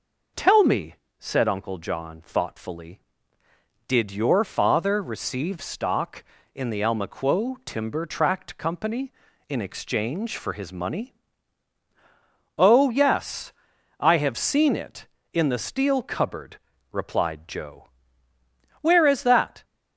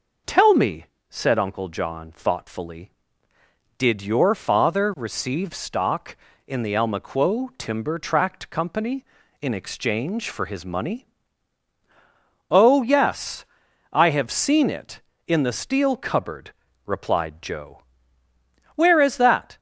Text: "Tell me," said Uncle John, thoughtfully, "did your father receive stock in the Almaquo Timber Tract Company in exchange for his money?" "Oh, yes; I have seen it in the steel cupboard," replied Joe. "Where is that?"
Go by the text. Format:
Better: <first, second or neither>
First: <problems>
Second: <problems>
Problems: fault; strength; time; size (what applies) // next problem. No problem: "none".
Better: neither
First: none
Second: none